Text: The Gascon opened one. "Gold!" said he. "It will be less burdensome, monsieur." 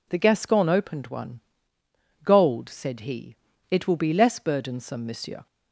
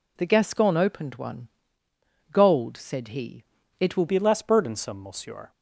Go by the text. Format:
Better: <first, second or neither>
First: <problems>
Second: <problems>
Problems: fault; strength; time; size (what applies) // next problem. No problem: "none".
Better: first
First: none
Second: changes voice at "be"; from 4.0 s on; 1.5 s long